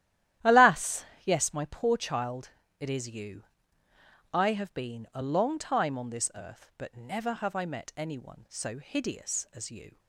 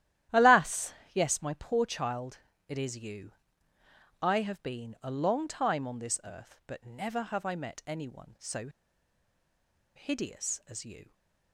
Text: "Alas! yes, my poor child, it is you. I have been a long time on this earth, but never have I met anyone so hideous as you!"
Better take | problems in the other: first | starts louder than the rest; strong; until 1.5 s; 12.5 dB; strong in the first // pauses between "so" and "hideous"; strong; at 8.6 s; 1.2 s long

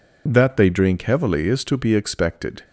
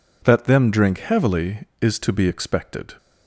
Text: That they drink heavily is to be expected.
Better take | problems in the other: first | says "them" for "they"; at 0.4 s

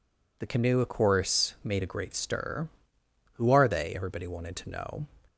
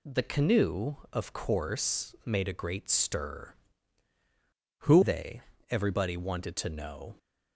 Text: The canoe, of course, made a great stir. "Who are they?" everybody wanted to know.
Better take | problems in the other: first | skips "are"; at 5.0 s

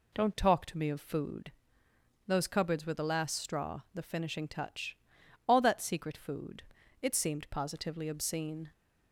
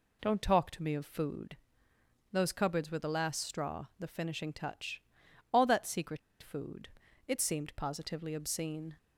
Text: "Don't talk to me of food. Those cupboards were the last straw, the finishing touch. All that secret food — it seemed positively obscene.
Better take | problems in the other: first | pauses between "secret" and "food"; slight; at 6.1 s; 0.23 s long

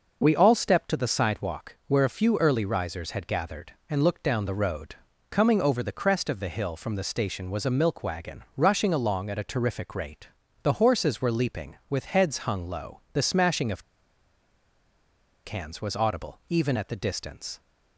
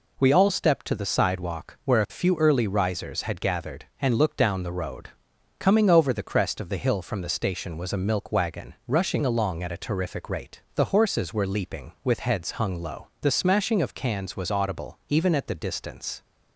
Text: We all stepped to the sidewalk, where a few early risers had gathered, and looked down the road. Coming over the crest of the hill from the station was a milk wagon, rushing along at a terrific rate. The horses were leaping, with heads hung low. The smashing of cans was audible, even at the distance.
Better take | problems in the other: second | pauses between "of" and "cans"; strong; at 13.8 s; 1.6 s long

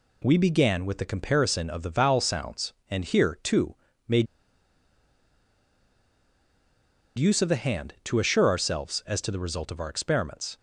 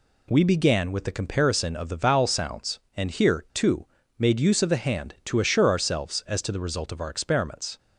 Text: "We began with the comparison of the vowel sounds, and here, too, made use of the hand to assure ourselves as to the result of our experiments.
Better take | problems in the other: second | pauses between "made" and "use"; strong; at 4.2 s; 2.9 s long

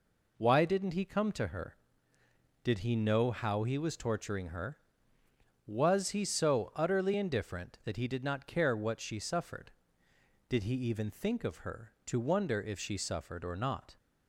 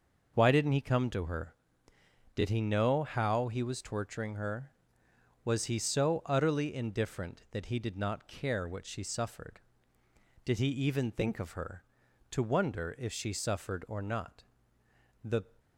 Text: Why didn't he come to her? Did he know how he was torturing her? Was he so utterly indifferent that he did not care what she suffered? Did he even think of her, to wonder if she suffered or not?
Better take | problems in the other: first | goes on to say "The"; slight; from 15.2 s on; 0.20 s long

